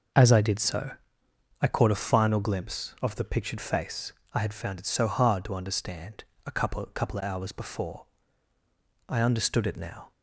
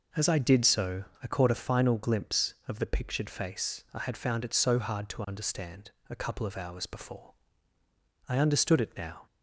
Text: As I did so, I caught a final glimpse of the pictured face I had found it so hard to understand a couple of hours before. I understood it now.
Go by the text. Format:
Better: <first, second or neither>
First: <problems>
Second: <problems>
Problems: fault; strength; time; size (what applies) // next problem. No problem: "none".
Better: second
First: starts louder than the rest; noticeable; until 1.8 s; 6 dB // pauses between "face" and "I"; slight; at 4.1 s; 0.22 s long // pauses between "understand" and "a"; slight; at 6.2 s; 0.20 s long // says "couple" twice; at 6.9 s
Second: pauses between "understand" and "a"; slight; at 5.8 s; 0.18 s long